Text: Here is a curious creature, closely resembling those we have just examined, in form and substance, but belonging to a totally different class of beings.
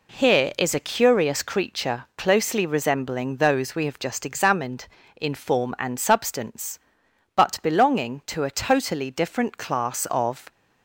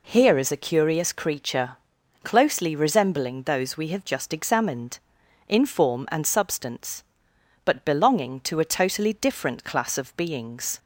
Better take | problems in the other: second | stops before "beings"; at 10.5 s

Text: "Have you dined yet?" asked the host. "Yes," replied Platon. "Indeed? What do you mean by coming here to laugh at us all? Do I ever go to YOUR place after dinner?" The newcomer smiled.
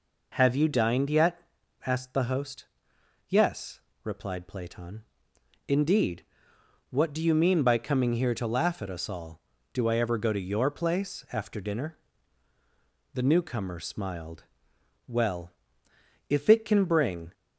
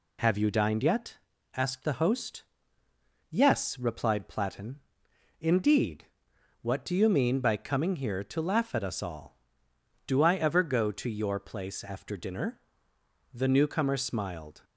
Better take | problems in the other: second | goes on to say "Well if it can bring"; strong; from 15.0 s on; 2.2 s long

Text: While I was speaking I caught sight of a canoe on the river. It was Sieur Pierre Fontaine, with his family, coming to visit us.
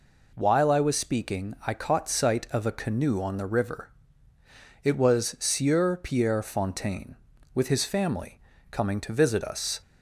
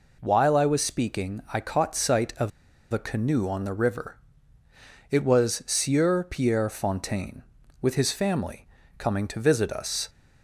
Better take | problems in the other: first | pauses between "of" and "a"; at 2.5 s; 0.40 s long

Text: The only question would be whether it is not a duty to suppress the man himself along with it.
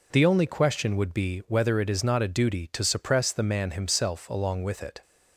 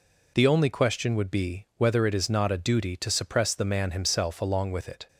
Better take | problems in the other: neither | none

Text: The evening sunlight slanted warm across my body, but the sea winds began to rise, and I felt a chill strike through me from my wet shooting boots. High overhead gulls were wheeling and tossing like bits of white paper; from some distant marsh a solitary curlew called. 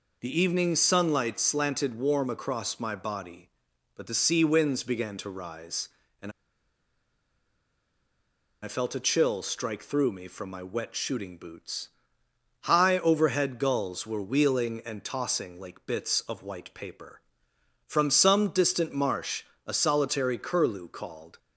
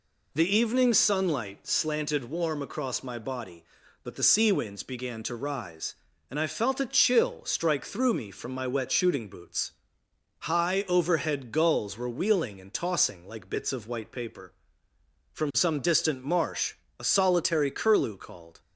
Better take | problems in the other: second | pauses between "and" and "I"; strong; at 6.2 s; 2.3 s long // pauses between "marsh" and "a"; slight; at 19.4 s; 0.20 s long; slight in the second

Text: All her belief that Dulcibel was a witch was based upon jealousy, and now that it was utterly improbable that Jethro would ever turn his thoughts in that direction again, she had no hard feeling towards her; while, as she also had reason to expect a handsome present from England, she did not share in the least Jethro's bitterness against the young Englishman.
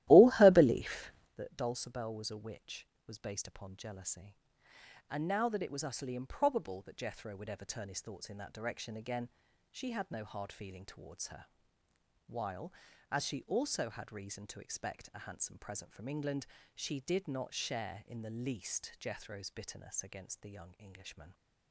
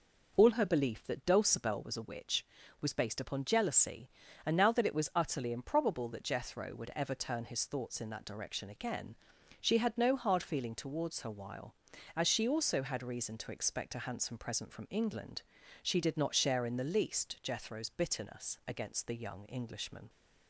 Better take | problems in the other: second | starts louder than the rest; strong; until 1.3 s; 15 dB

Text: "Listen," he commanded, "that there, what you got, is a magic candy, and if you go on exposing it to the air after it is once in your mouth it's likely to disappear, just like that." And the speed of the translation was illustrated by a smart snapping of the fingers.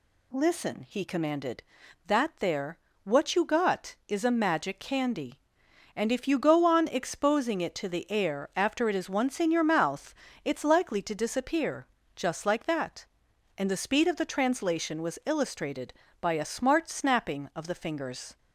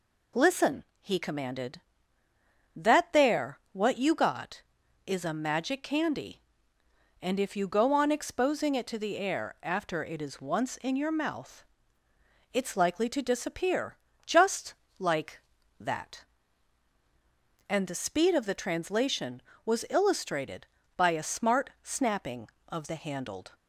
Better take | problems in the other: first | pauses between "mouth" and "it's"; noticeable; at 11.6 s; 0.88 s long; slight in the first // pauses between "just" and "like"; slight; at 14.7 s; 0.24 s long // says "handled" for "fingers"; at 22.9 s

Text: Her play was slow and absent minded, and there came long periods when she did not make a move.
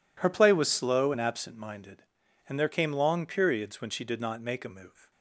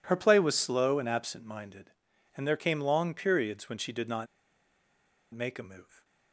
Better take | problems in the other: first | pauses between "not" and "make"; at 4.2 s; 1.0 s long

